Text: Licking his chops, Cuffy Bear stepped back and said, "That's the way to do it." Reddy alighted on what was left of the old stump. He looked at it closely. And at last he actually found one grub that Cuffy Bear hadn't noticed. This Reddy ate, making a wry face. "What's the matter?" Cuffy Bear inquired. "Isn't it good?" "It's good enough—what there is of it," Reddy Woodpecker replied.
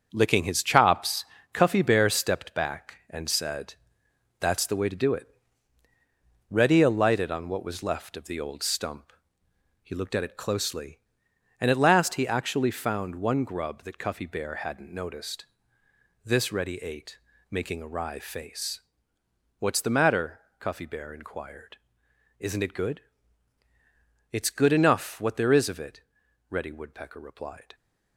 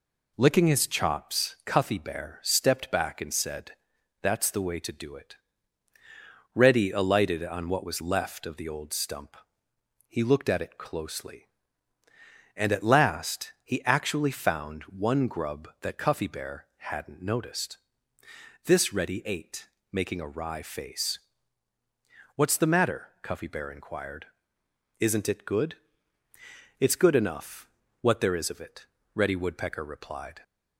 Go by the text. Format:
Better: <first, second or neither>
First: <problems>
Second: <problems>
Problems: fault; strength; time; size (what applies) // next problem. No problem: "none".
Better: second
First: gets quieter; strong; throughout; 7.5 dB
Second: none